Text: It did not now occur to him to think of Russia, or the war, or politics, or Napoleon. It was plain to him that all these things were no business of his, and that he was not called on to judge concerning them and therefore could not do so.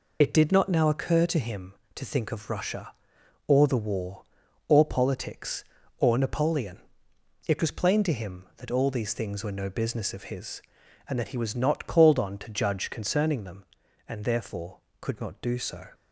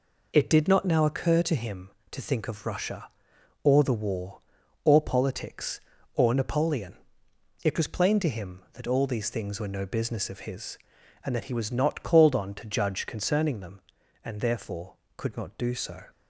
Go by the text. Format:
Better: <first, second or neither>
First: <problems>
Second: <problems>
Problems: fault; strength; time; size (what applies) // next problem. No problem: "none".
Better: second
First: loses the start of "It"; at 0.2 s; 25 ms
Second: none